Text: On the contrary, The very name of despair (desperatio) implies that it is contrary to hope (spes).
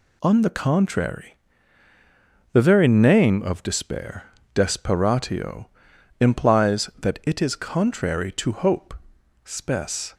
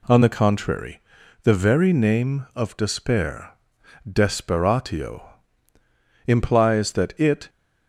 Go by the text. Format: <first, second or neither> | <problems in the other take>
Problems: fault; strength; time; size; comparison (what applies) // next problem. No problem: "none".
first | stops before "is contrary to hope spes"; at 7.4 s